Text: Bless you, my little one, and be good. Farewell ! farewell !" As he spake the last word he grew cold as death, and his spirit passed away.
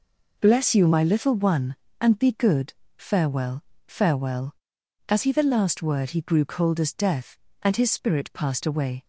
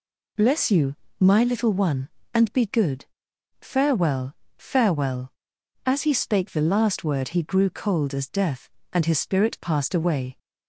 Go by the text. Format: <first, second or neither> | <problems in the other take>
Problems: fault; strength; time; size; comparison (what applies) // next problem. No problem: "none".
second | skips "spake"; at 5.3 s